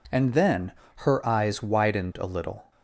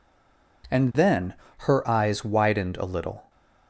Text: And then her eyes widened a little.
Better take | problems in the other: first | stays silent before the first word; slight; until 0.6 s; 0.6 s long // pauses between "then" and "her"; slight; at 1.3 s; 0.26 s long; slight in the first

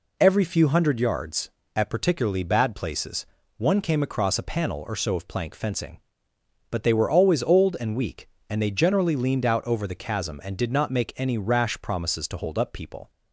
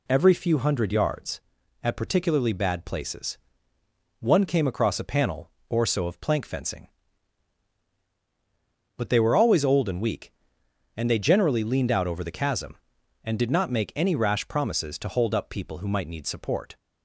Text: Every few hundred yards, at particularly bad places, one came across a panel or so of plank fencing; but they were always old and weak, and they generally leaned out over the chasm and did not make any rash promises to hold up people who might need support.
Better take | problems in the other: second | stops before "who might need support"; at 13.0 s

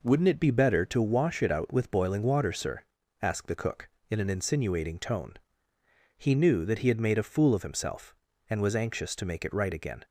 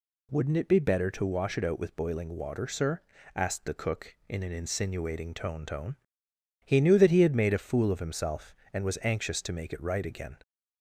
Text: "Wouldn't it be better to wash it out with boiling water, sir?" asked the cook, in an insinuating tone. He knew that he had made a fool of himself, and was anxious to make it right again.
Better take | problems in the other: first | says "tone" twice; at 5.6 s

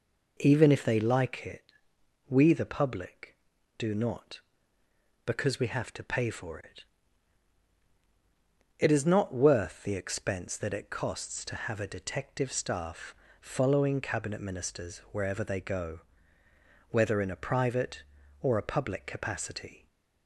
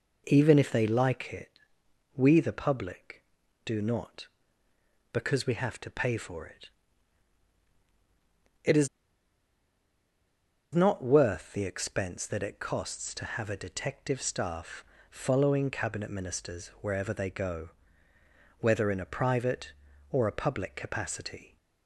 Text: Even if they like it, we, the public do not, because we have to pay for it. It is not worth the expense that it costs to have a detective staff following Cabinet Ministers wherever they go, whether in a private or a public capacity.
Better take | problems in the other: first | pauses between "is" and "not"; strong; at 8.8 s; 1.8 s long // pauses between "staff" and "following"; slight; at 14.8 s; 0.26 s long; slight in the first

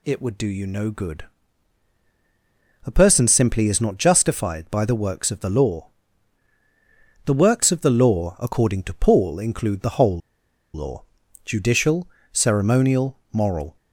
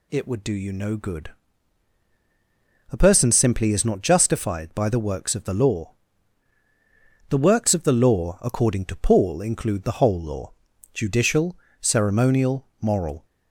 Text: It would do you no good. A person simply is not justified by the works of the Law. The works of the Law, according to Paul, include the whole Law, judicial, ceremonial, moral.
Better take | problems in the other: second | pauses between "whole" and "Law"; noticeable; at 10.1 s; 0.55 s long

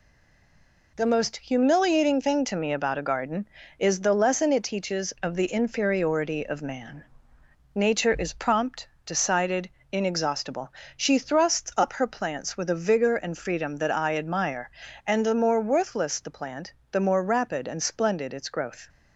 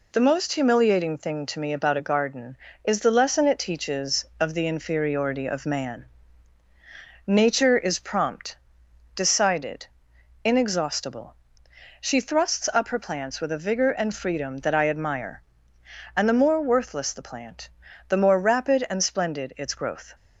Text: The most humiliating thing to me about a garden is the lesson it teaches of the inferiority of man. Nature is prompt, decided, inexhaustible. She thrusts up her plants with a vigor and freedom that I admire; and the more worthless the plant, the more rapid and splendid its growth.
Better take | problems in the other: second | stays silent before the first word; slight; until 0.9 s; 0.9 s long

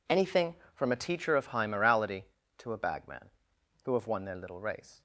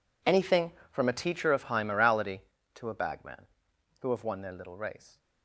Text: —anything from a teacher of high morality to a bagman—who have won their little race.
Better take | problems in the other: first | gets quieter; strong; throughout; 19 dB

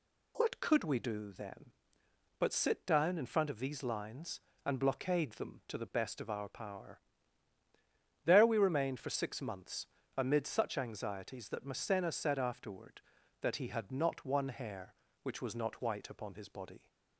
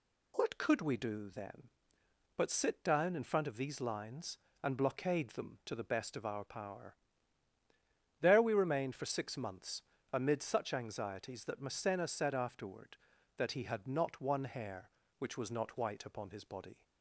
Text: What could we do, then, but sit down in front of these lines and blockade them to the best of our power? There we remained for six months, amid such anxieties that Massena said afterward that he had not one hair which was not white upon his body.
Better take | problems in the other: neither | none

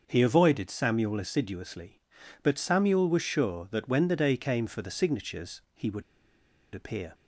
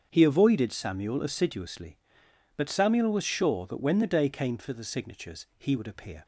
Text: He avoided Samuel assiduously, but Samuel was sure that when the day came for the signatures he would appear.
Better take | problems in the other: second | starts louder than the rest; until 1.0 s; 6.5 dB; strong in the second // pauses between "would" and "appear"; noticeable; at 6.0 s; 0.72 s long

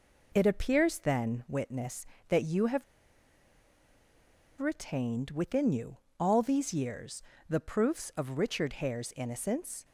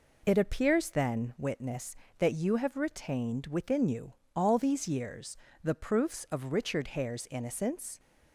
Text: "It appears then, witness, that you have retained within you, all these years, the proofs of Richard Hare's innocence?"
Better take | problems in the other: second | pauses between "have" and "retained"; strong; at 2.8 s; 1.7 s long

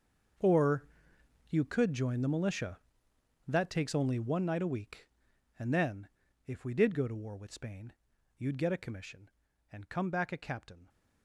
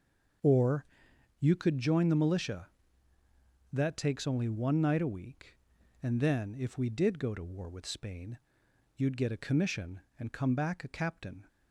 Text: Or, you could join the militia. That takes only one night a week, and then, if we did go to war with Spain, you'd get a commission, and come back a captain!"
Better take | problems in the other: second | gets quieter; strong; throughout; 16 dB // starts louder than the rest; until 2.0 s; 6.5 dB; also in the second

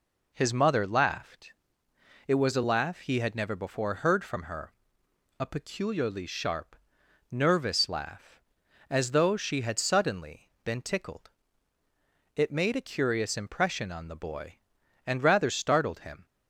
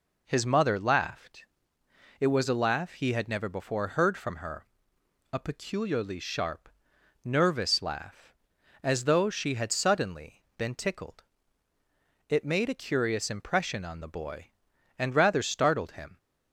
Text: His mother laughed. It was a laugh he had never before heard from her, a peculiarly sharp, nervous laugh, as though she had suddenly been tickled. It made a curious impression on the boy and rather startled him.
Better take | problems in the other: neither | pauses between "suddenly" and "been"; slight; the same in both

